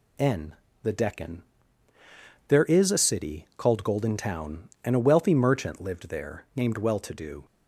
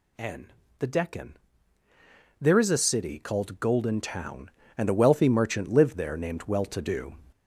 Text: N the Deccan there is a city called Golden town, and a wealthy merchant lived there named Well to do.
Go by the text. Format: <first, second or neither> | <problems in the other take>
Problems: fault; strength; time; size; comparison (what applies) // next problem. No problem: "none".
first | gets louder; throughout; 6.5 dB // pauses between "N" and "the"; slight; at 0.5 s; 0.26 s long; slight in the first // pauses between "Deccan" and "there"; at 1.3 s; 1.0 s long; also in the first